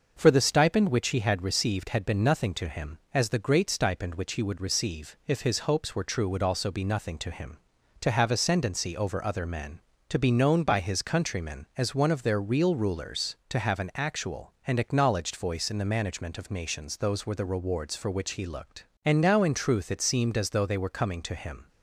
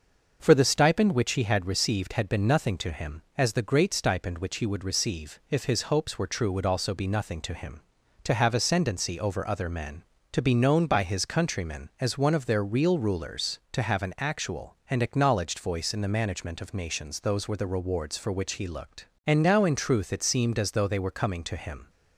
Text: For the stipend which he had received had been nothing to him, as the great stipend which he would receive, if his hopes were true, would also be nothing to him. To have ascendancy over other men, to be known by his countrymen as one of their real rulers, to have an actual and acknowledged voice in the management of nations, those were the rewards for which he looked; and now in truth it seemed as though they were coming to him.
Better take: neither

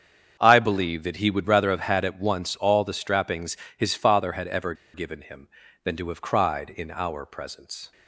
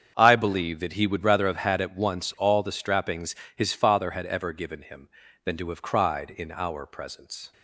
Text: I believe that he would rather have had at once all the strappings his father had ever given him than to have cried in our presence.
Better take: second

